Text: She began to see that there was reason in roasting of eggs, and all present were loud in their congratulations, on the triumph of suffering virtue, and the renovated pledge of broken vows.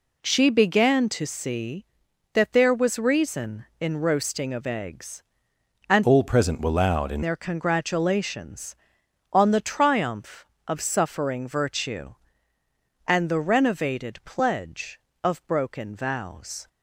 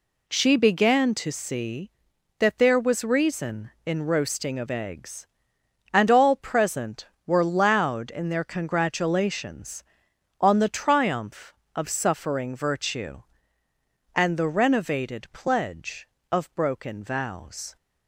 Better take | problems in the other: second | changes voice from "all" to "in"; from 6.0 to 7.2 s; 1.2 s long

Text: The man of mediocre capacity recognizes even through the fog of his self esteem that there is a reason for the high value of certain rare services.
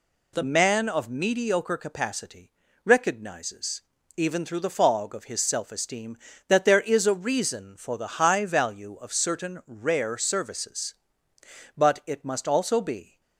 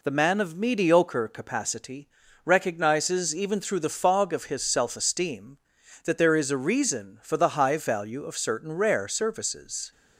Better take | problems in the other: second | pauses between "capacity" and "recognizes"; slight; at 2.5 s; 0.34 s long; slight in the second // pauses between "recognizes" and "even"; slight; at 3.8 s; 0.34 s long // goes on to say "But it must also be"; from 11.7 s on; 1.4 s long

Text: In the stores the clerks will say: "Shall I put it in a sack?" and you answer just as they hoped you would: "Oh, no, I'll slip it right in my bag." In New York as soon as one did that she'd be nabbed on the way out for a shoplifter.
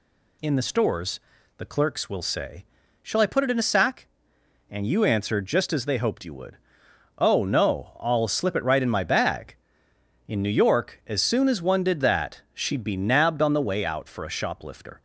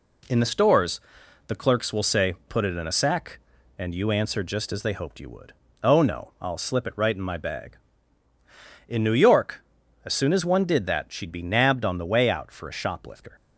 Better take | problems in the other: first | pauses between "stores" and "the"; noticeable; at 0.9 s; 0.48 s long; also in the first // skips "Shall I"; at 2.4 s

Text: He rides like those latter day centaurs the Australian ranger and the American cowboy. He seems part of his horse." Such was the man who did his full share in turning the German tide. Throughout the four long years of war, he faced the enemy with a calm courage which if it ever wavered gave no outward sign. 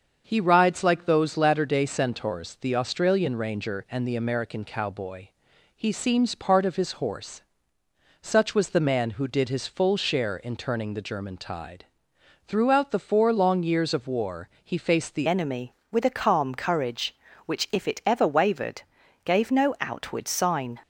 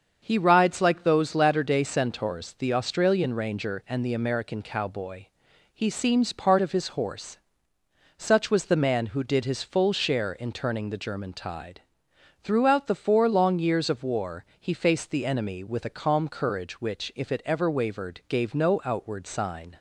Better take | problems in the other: second | starts louder than the rest; until 1.2 s; 6.5 dB; also in the second // changes voice at "enemy"; from 15.2 s on; 5.5 s long // pauses between "wavered" and "gave"; at 18.8 s; 0.44 s long

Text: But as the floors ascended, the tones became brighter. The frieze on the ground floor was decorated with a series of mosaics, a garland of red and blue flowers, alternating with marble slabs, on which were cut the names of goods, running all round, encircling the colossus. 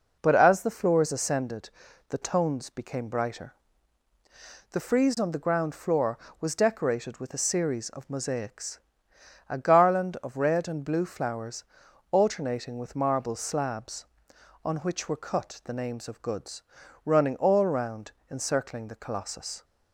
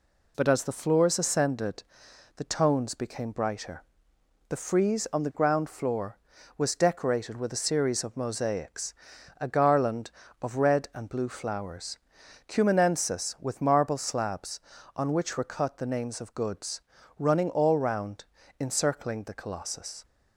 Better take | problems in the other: first | says "cumanensis" for "alternating"; at 12.4 s

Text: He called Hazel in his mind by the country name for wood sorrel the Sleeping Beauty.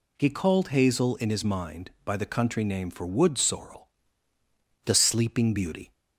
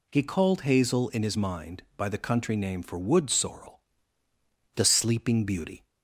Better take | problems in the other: neither | pauses between "sorrel" and "the"; noticeable; the same in both

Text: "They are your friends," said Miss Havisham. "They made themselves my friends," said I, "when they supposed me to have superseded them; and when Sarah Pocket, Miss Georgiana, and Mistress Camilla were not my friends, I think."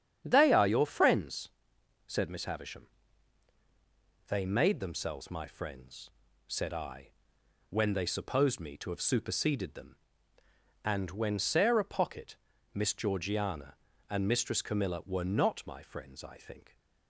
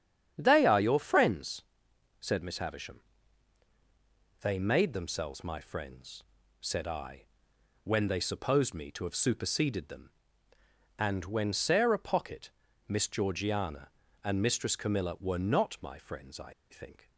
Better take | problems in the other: first | starts louder than the rest; strong; until 1.3 s; 8.5 dB; strong in the first // pauses between "I" and "think"; slight; at 16.5 s; 0.16 s long

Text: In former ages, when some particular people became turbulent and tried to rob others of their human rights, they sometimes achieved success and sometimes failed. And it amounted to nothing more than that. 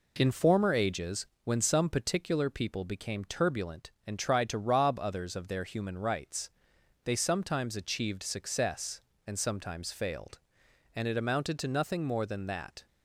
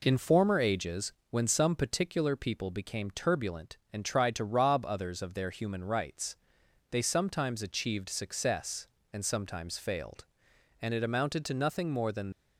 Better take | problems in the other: first | stops before "that"; at 12.3 s

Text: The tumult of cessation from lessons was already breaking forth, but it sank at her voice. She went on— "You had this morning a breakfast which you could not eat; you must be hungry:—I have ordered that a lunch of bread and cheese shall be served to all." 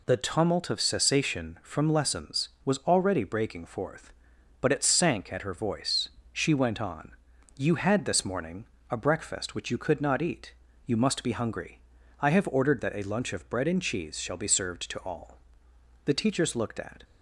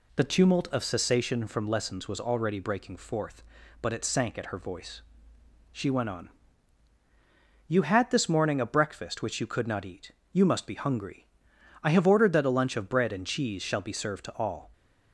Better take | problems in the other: second | pauses between "morning" and "a"; slight; at 8.6 s; 0.24 s long // goes on to say "The teachers looked at"; noticeable; from 16.0 s on; 0.98 s long

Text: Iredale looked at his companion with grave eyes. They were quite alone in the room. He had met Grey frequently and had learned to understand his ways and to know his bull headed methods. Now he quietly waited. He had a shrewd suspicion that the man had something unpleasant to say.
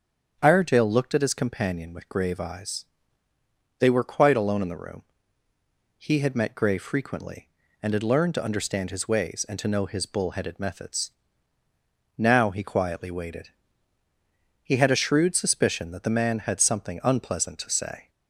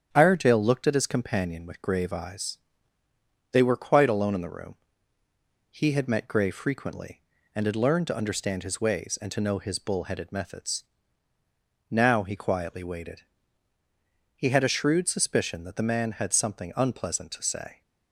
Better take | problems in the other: first | gets quieter; throughout; 3.5 dB // starts louder than the rest; strong; until 1.1 s; 8.5 dB; strong in the first

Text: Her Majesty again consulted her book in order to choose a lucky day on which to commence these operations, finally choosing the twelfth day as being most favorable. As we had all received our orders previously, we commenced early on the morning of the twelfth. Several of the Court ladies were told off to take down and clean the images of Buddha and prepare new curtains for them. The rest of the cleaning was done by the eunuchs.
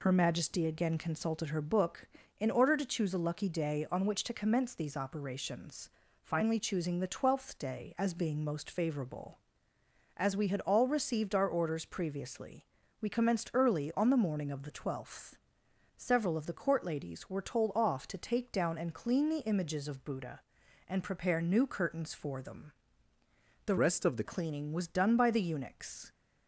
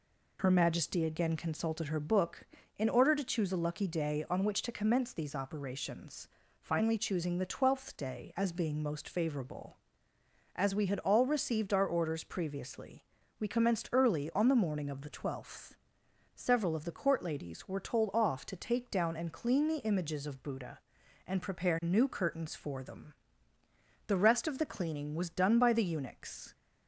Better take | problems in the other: second | changes voice from "rest" to "the"; from 23.7 to 24.2 s; 0.5 s long

